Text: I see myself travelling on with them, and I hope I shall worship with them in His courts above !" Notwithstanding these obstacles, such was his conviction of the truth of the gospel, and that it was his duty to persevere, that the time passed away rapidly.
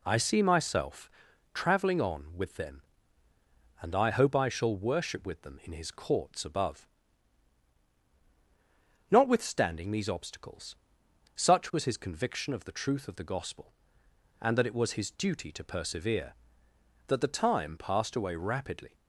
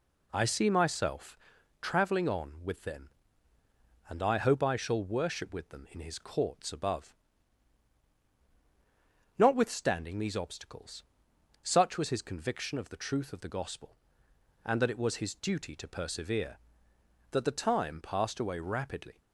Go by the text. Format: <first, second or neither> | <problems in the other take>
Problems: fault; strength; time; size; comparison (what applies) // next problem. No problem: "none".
neither | pauses between "myself" and "travelling"; the same in both